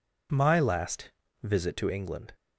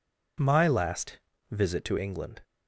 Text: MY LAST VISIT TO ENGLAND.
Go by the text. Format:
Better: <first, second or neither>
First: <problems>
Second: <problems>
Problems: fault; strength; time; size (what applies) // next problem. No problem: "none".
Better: neither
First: pauses between "LAST" and "VISIT"; slight; at 1.1 s; 0.32 s long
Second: pauses between "LAST" and "VISIT"; slight; at 1.1 s; 0.32 s long